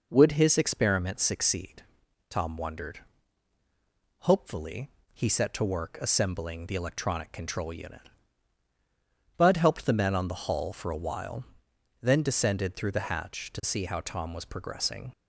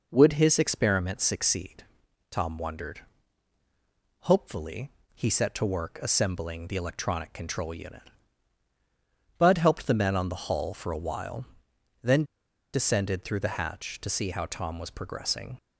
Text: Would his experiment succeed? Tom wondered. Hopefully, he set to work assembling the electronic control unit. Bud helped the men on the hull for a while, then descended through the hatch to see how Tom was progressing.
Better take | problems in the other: first | pauses between "then" and "descended"; noticeable; at 12.2 s; 0.49 s long

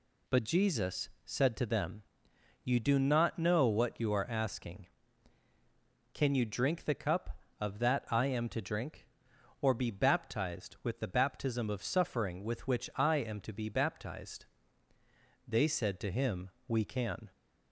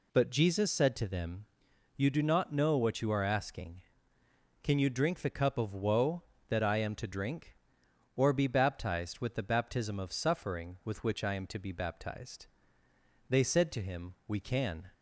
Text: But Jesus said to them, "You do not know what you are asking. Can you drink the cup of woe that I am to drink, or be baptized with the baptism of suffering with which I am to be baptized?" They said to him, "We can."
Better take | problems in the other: second | pauses between "Jesus" and "said"; slight; at 1.0 s; 0.16 s long // skips "woe"; at 7.7 s

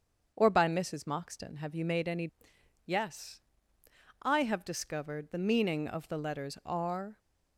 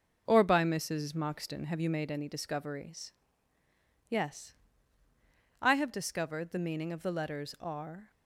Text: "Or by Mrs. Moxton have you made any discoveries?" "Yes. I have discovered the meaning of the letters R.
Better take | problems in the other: second | starts louder than the rest; until 1.3 s; 7 dB; noticeable in the second // skips "discoveries"; at 2.5 s

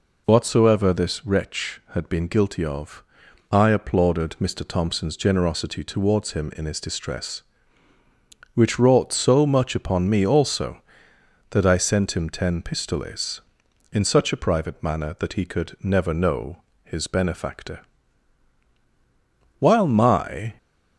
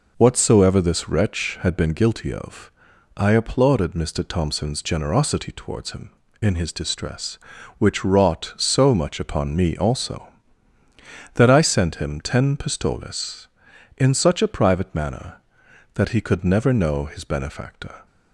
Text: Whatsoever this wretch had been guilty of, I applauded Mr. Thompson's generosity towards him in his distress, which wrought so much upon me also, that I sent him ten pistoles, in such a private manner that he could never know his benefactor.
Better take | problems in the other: second | pauses between "know" and "his"; slight; at 16.5 s; 0.26 s long // goes on to say "While my"; noticeable; from 19.5 s on; 0.96 s long

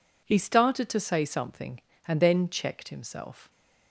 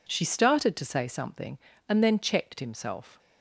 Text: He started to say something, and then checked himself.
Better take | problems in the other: first | says "She" for "He"; at 0.0 s

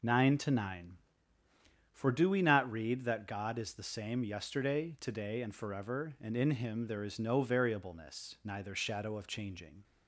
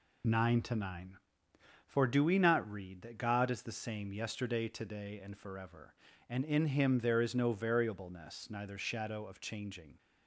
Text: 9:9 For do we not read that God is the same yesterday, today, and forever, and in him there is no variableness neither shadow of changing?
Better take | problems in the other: neither | none

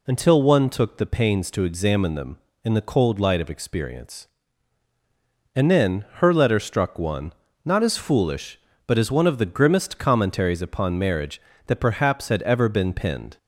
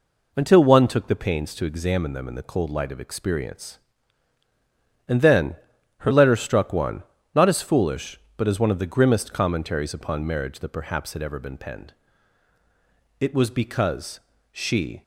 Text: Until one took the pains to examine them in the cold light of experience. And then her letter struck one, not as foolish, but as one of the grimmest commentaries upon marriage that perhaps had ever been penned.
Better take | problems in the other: first | pauses between "then" and "her"; at 5.5 s; 0.42 s long // goes on to say "It was because she"; strong; from 13.2 s on; 1.8 s long

